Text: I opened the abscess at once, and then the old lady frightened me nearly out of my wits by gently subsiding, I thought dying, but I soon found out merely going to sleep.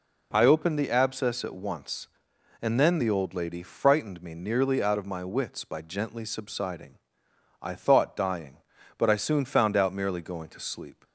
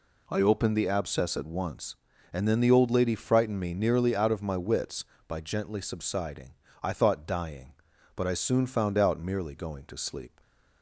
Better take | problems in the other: neither | none

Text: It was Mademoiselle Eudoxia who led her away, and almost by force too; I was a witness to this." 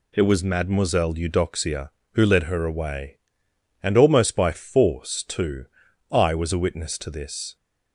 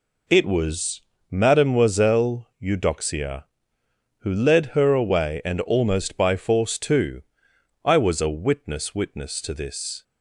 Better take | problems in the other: first | pauses between "was" and "Mademoiselle"; slight; at 1.0 s; 0.28 s long // says "witness" twice; at 8.9 s

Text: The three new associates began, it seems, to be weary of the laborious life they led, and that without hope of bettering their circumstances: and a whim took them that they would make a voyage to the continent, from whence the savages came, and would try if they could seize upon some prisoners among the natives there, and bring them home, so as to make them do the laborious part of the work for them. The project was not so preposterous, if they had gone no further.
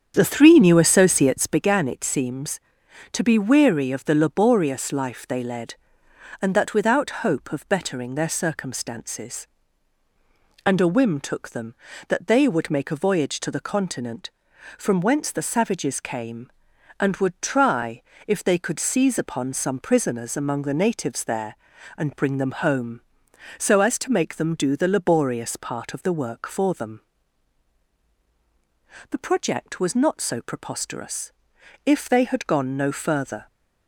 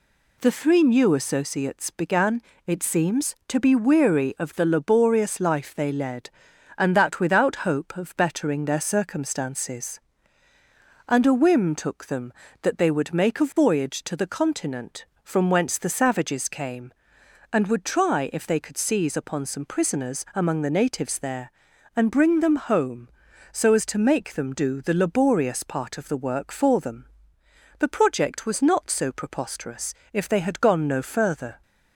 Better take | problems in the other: second | starts louder than the rest; strong; until 1.6 s; 8 dB // pauses between "try" and "if"; slight; at 17.9 s; 0.28 s long

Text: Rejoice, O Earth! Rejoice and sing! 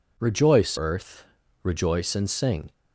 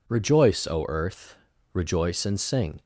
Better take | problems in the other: second | skips "O"; at 0.7 s

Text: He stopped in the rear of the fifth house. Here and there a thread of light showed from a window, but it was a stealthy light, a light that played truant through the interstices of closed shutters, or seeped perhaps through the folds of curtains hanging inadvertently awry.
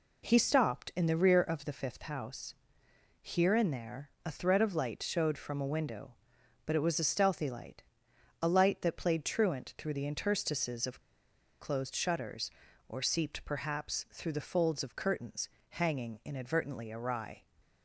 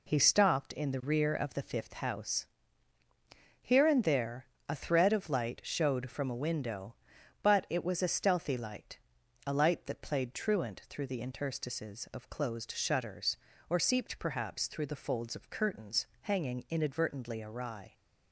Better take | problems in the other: second | pauses between "there" and "a"; slight; at 4.0 s; 0.16 s long; slight in the second // pauses between "of" and "closed"; noticeable; at 11.0 s; 0.59 s long // pauses between "curtains" and "hanging"; slight; at 15.4 s; 0.22 s long

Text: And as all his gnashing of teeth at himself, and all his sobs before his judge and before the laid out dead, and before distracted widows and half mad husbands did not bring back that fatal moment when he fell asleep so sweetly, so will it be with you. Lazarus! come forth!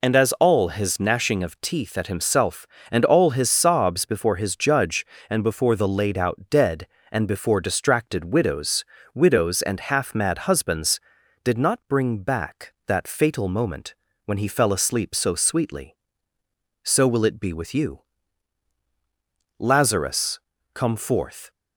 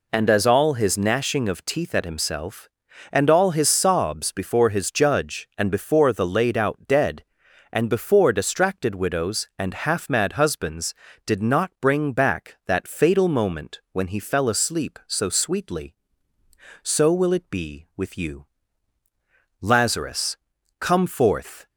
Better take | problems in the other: second | says "widows" twice; at 9.1 s // pauses between "moment" and "when"; slight; at 13.9 s; 0.30 s long

